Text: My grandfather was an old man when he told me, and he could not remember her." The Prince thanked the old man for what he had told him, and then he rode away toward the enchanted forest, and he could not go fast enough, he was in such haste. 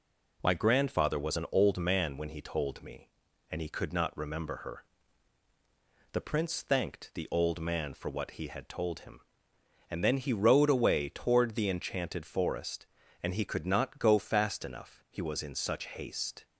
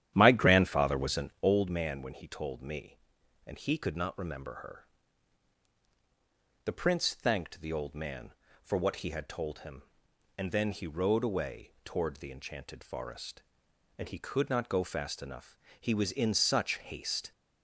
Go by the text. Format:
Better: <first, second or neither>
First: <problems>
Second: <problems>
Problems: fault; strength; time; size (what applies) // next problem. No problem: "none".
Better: first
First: none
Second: starts louder than the rest; strong; until 1.5 s; 11 dB